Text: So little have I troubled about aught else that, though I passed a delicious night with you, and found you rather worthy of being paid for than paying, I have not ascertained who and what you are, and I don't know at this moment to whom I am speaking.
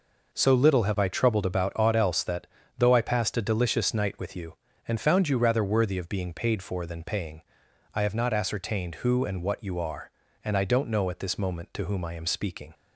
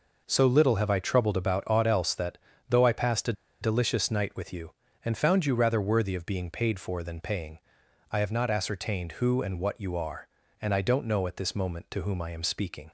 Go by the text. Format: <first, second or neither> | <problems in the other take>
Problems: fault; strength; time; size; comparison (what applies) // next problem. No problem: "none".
first | pauses between "a" and "delicious"; slight; at 3.3 s; 0.28 s long